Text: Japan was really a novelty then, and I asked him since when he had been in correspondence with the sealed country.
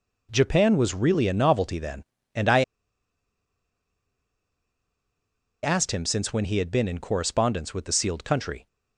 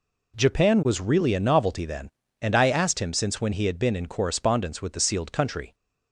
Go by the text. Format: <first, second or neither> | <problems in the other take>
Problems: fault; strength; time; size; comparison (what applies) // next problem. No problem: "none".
second | pauses between "I" and "asked"; strong; at 2.6 s; 3.0 s long